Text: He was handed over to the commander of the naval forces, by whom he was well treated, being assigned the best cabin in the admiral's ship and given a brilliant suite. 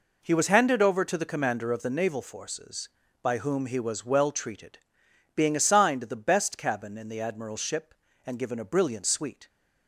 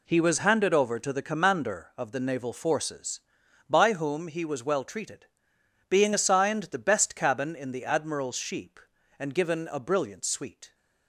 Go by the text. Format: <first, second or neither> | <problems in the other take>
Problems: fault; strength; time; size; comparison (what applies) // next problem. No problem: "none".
first | says "sheep" for "ship"; at 8.3 s